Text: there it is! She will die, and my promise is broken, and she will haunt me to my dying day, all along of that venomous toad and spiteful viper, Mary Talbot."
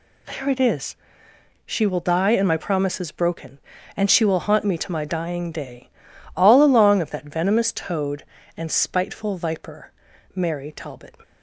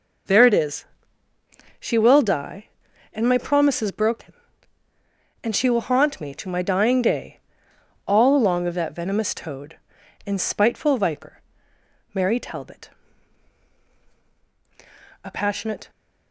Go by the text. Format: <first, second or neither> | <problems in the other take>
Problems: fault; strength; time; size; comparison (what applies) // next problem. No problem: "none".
first | goes on to say "A passionate"; noticeable; from 15.2 s on; 0.66 s long